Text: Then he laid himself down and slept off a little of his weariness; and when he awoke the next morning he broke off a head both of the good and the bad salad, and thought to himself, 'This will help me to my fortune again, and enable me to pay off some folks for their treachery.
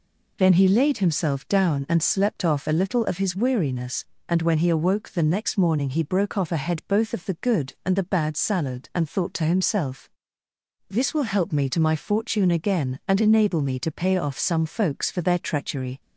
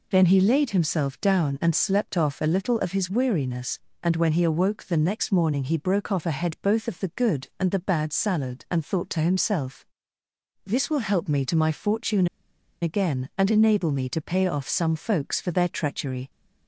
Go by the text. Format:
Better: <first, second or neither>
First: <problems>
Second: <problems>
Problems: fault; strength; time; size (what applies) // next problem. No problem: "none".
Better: first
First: none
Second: pauses between "fortune" and "again"; noticeable; at 12.2 s; 0.55 s long